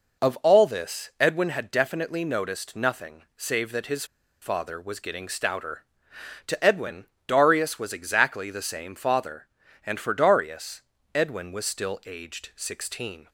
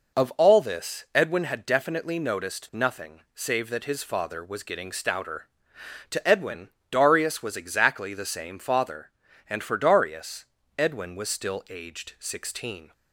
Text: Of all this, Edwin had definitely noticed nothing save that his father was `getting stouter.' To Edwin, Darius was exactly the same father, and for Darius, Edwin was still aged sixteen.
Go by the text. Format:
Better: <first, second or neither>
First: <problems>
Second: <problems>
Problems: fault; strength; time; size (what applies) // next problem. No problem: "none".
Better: second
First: pauses between "his" and "father"; at 4.0 s; 0.37 s long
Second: none